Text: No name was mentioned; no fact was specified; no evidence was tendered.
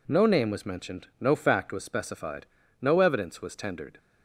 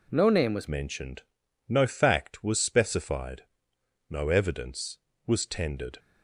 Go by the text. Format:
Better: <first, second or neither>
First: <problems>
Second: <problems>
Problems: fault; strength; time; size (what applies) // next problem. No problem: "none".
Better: first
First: none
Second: changes voice at "mentioned"; from 0.6 s on; 5.3 s long